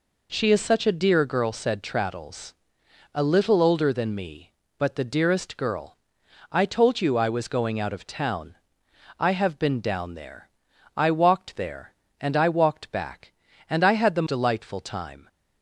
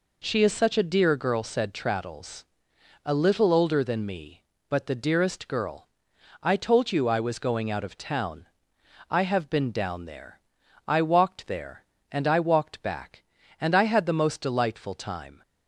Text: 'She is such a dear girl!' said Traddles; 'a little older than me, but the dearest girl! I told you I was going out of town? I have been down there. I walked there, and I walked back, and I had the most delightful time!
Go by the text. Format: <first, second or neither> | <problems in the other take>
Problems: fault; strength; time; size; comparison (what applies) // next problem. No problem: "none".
second | skips "most"; at 14.2 s